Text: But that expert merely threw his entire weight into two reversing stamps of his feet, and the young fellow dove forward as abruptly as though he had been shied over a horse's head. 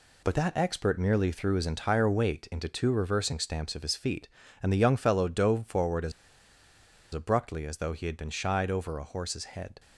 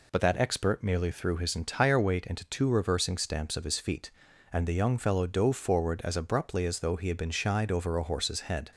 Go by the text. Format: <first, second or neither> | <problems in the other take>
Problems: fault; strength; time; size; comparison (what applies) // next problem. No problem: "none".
second | pauses between "as" and "abruptly"; at 6.1 s; 1.0 s long